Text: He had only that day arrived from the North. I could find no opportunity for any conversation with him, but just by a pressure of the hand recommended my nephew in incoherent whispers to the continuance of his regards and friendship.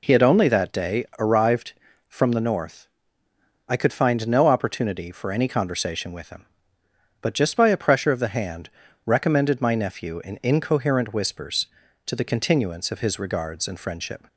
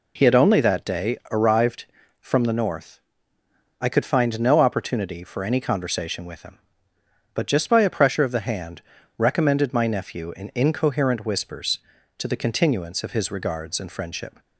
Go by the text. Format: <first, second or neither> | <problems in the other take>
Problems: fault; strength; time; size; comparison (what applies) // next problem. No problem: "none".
neither | pauses between "hand" and "recommended"; the same in both